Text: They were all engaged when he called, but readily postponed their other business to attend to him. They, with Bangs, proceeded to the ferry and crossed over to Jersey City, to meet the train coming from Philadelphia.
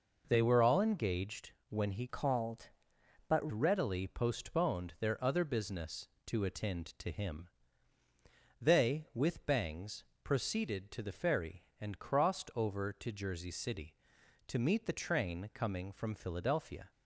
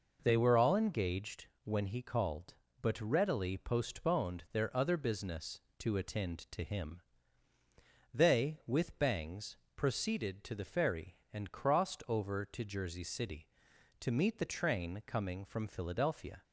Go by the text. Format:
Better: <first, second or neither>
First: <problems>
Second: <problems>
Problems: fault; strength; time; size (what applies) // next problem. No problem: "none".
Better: second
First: pauses between "engaged" and "when"; slight; at 1.5 s; 0.18 s long // changes voice from "called" to "but"; from 2.0 to 3.5 s; 1.5 s long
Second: pauses between "engaged" and "when"; slight; at 1.4 s; 0.18 s long